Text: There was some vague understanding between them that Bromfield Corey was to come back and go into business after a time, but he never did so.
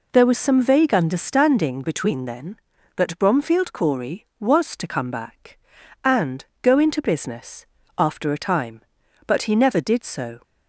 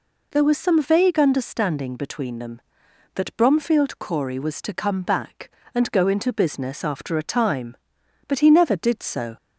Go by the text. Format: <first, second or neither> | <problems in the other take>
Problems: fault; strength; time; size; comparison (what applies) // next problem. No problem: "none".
second | says "then" for "them"; at 2.2 s // pauses between "and" and "go"; slight; at 6.4 s; 0.18 s long // pauses between "business" and "after"; slight; at 7.6 s; 0.32 s long